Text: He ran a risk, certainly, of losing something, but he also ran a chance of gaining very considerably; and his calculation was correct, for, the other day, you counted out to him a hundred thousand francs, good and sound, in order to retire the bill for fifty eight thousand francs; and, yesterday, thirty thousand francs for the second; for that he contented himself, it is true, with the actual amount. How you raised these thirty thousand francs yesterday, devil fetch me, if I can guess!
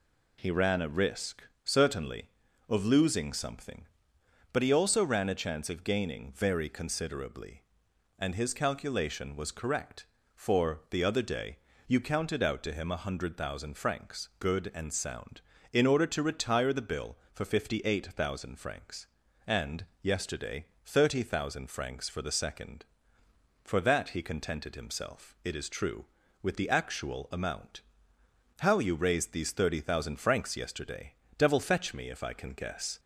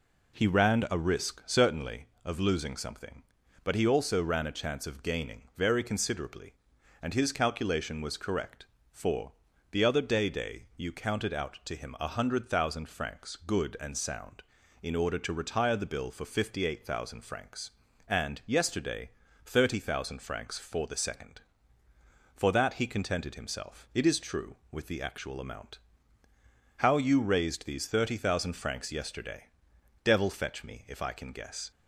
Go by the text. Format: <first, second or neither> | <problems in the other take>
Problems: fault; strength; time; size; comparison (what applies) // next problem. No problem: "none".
first | says "day" twice; at 10.2 s